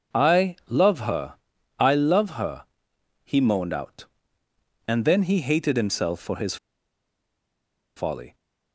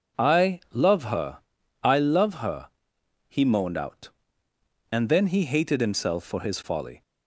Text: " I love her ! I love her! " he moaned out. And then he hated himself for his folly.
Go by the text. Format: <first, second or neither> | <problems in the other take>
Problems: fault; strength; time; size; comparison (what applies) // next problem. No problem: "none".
second | starts louder than the rest; noticeable; until 1.3 s; 6 dB; noticeable in the second // pauses between "his" and "folly"; strong; at 6.5 s; 1.3 s long